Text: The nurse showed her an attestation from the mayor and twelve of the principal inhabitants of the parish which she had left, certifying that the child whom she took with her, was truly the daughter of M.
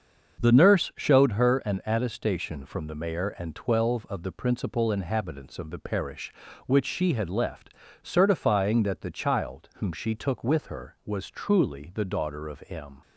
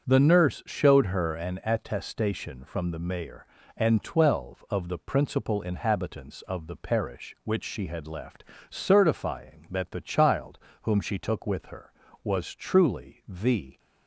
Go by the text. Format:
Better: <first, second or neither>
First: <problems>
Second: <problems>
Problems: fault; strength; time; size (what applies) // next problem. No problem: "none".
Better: first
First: starts louder than the rest; until 1.4 s; 7 dB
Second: starts louder than the rest; strong; until 1.1 s; 7.5 dB // pauses between "child" and "whom"; slight; at 10.5 s; 0.24 s long // stops before "daughter of M"; at 13.7 s